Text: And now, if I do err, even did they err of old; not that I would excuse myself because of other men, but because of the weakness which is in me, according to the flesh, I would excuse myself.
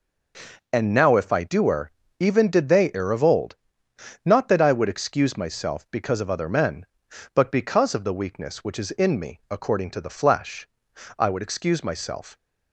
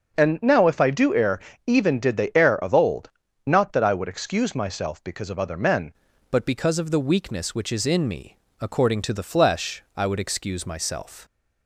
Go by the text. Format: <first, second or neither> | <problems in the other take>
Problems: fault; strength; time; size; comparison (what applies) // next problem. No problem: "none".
first | starts louder than the rest; until 1.2 s; 6.5 dB // changes voice at "but"; from 6.2 s on; 5.0 s long